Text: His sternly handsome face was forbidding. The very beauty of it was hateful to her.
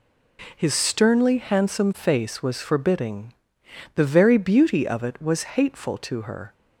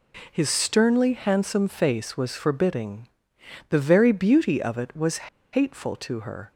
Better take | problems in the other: first | pauses between "was" and "hateful"; slight; at 5.2 s; 0.24 s long

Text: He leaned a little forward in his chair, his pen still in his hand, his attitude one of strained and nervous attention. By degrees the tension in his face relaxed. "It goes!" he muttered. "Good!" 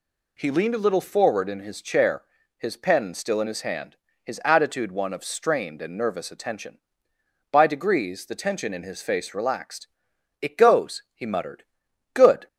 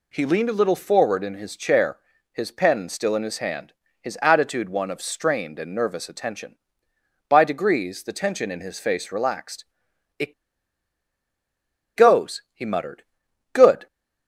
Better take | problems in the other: first | pauses between "It" and "goes"; strong; at 10.3 s; 1.6 s long

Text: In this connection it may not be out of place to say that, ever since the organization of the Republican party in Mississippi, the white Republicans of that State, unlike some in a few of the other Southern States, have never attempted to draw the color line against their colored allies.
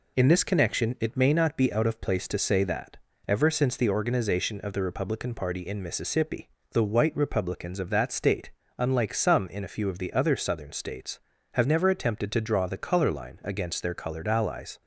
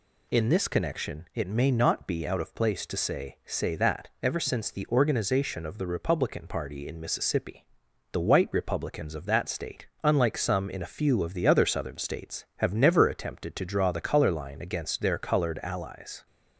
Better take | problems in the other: first | says "say" twice; at 3.4 s

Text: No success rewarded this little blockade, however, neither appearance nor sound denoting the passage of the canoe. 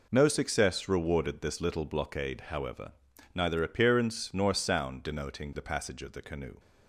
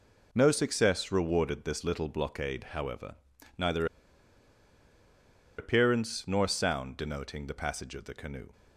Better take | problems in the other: first | pauses between "neither" and "appearance"; strong; at 3.8 s; 1.7 s long

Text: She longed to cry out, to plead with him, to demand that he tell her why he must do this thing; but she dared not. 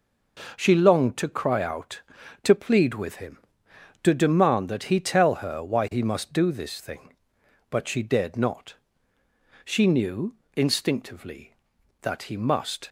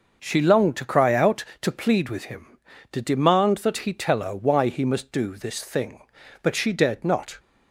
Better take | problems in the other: second | goes on to say "She knew instinctively that he must"; strong; from 9.6 s on; 3.2 s long

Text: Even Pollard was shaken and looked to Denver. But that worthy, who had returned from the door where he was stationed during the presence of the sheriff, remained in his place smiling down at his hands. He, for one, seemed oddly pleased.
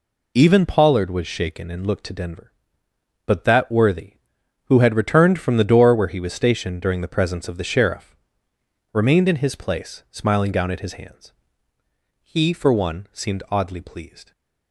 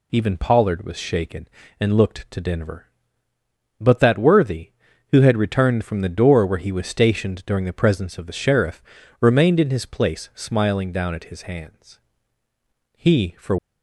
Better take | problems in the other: first | stops before "one seemed oddly pleased"; at 13.5 s

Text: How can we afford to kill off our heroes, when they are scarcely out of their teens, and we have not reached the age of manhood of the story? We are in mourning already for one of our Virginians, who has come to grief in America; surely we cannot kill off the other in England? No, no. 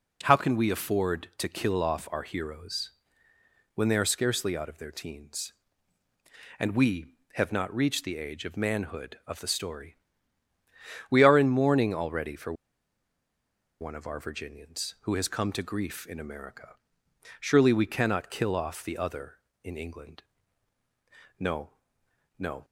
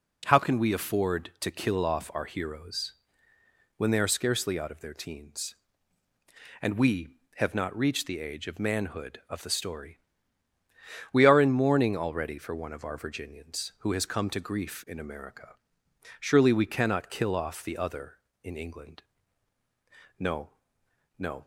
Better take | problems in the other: second | pauses between "for" and "one"; strong; at 12.5 s; 1.2 s long

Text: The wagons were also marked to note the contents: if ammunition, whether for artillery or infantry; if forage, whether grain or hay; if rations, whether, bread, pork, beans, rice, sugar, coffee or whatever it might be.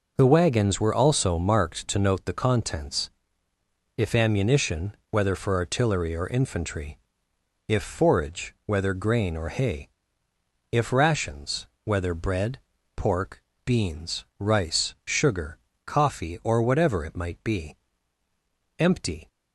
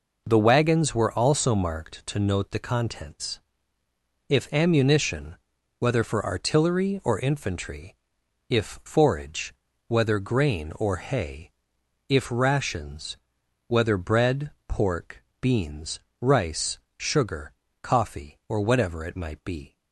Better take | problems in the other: second | goes on to say "Empty"; slight; from 18.7 s on; 0.48 s long

